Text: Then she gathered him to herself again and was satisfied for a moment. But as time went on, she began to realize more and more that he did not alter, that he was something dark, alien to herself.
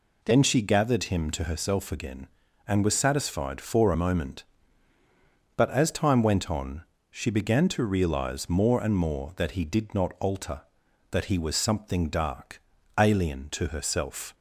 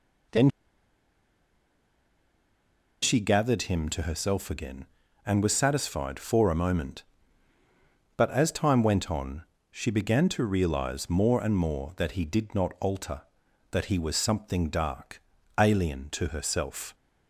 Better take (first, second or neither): first